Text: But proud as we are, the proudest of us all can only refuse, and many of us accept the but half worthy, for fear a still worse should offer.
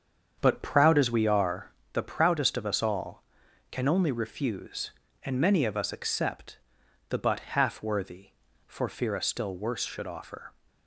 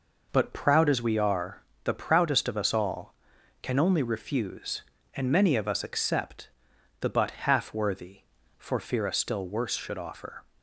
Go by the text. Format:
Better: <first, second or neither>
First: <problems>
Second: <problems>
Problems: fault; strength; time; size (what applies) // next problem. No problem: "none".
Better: second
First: starts louder than the rest; strong; until 1.9 s; 7.5 dB // pauses between "accept" and "the"; noticeable; at 6.5 s; 0.50 s long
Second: pauses between "accept" and "the"; noticeable; at 6.5 s; 0.50 s long